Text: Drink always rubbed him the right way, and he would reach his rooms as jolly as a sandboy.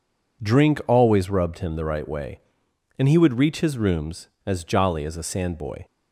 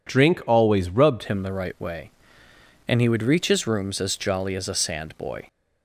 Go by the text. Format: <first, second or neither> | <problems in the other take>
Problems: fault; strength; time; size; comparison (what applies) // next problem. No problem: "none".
first | changes voice at "him"; from 1.2 s on; 4.2 s long